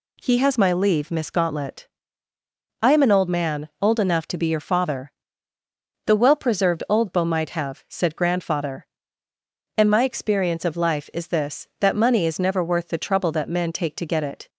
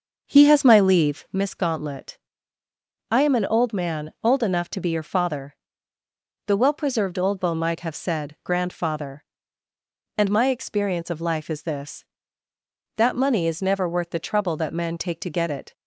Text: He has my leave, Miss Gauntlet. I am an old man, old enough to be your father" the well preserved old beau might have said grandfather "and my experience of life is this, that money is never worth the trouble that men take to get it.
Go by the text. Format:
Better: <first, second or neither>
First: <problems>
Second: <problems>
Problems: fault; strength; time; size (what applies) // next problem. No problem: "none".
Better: first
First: pauses between "father" and "the"; noticeable; at 5.1 s; 0.94 s long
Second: starts louder than the rest; noticeable; until 1.4 s; 6 dB // pauses between "father" and "the"; noticeable; at 5.5 s; 0.90 s long